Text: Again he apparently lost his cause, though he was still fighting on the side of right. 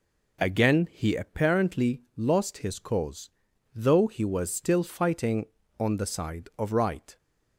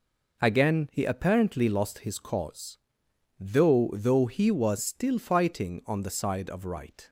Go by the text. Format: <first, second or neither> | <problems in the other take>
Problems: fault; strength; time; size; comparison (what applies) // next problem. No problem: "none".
first | says "though" twice; at 3.9 s